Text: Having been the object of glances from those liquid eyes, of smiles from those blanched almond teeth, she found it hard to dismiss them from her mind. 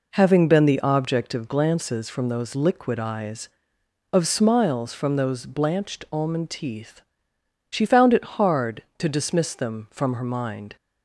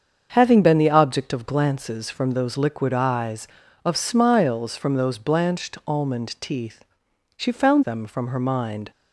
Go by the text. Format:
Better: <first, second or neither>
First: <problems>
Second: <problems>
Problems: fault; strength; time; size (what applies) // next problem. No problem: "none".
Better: first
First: none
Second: starts louder than the rest; strong; until 1.3 s; 7 dB // skips "it hard to dismiss"; at 7.8 s